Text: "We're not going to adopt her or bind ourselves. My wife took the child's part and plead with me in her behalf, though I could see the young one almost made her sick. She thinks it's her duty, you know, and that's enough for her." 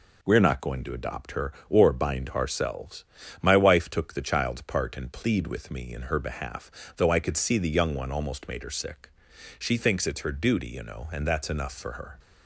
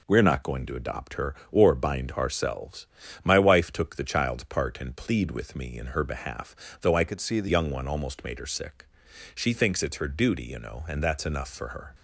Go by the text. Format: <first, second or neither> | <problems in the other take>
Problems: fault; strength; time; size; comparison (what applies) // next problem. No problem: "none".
first | changes voice from "could" to "the"; from 7.0 to 7.4 s; 0.4 s long